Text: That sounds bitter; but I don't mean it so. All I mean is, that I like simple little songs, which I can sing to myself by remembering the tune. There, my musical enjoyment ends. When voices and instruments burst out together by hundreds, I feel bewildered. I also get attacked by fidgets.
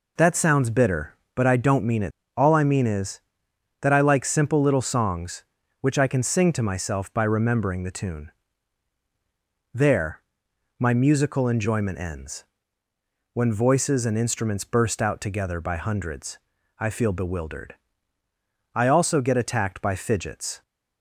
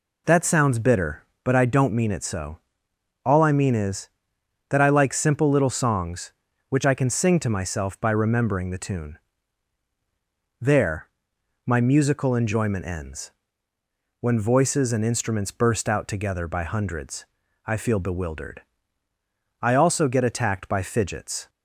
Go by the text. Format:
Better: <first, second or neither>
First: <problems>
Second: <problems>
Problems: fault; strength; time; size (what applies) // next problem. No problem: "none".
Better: second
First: skips "so"; at 2.2 s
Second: none